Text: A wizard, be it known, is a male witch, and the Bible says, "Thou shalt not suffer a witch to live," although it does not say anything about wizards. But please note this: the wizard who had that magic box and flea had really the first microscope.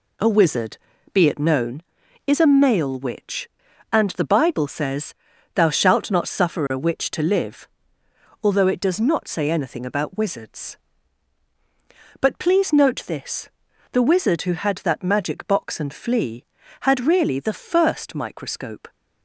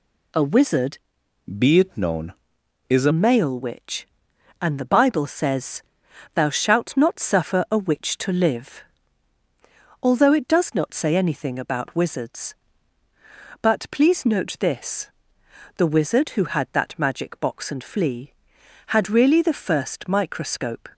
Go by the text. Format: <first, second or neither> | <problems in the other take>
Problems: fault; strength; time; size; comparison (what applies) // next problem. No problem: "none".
first | changes voice from "be" to "a"; from 1.5 to 3.1 s; 1.6 s long